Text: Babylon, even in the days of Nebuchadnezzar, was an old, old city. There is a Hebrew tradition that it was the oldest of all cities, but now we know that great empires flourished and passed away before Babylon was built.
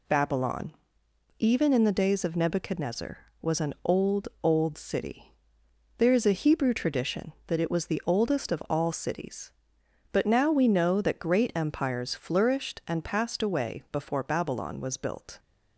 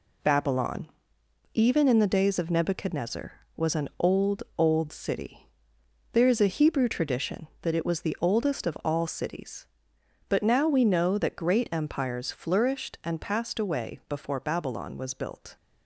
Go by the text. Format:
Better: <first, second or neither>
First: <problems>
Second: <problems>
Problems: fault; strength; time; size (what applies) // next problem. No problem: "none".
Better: first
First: none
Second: gets quieter; throughout; 6 dB